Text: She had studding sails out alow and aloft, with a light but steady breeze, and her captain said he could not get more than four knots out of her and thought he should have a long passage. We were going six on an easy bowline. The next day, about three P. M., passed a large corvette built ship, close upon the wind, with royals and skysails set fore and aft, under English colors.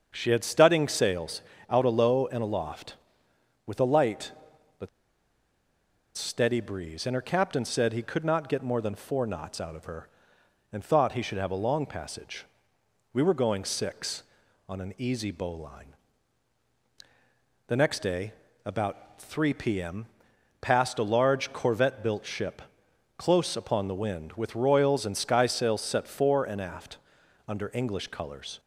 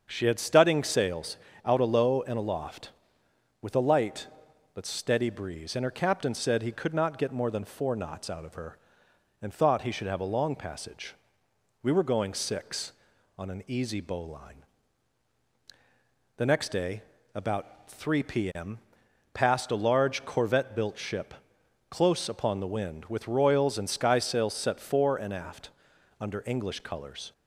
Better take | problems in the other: second | starts louder than the rest; until 1.1 s; 7 dB; also in the second // pauses between "sails" and "out"; slight; at 1.4 s; 0.28 s long; slight in the second // pauses between "but" and "steady"; strong; at 4.8 s; 1.2 s long

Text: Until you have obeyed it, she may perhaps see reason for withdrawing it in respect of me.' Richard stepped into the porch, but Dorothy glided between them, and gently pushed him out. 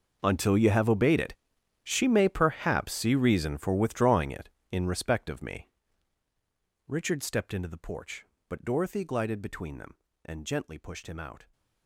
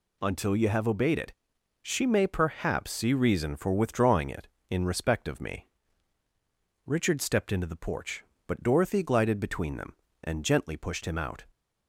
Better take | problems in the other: second | gets quieter; strong; throughout; 18.5 dB

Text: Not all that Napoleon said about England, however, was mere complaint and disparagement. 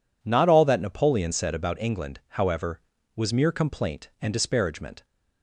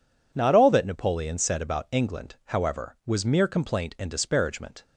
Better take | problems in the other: neither | none

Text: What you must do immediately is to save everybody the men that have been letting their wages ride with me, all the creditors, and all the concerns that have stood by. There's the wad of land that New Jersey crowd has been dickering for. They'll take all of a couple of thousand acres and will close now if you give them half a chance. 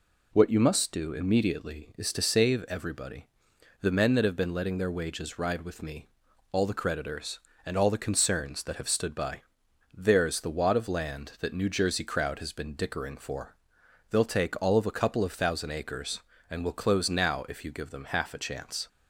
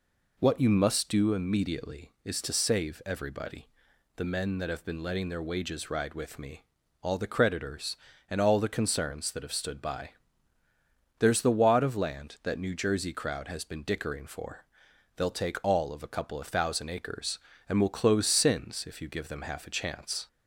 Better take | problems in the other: first | pauses between "everybody" and "the"; noticeable; at 3.6 s; 0.52 s long; noticeable in the first // says "sins" for "now"; at 18.2 s

